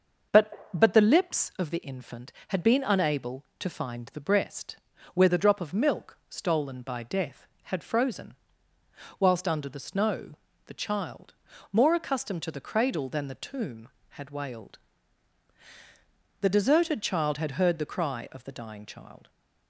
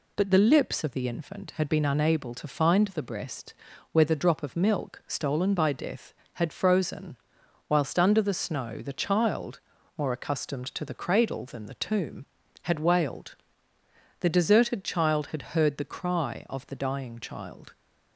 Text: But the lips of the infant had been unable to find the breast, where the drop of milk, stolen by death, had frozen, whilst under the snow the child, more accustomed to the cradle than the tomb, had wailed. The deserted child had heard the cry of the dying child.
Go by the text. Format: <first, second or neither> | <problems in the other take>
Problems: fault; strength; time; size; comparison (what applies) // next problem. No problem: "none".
second | says "But" twice; at 0.7 s // pauses between "snow" and "the"; slight; at 10.3 s; 0.32 s long